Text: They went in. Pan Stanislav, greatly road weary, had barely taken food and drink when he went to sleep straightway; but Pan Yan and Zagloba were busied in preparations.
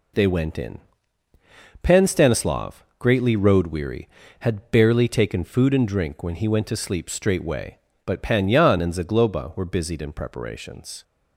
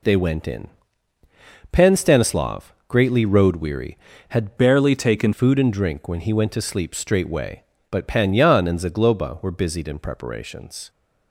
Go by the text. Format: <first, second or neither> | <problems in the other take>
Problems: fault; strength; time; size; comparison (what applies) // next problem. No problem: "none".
first | changes voice from "barely" to "taken"; from 4.5 to 5.3 s; 0.8 s long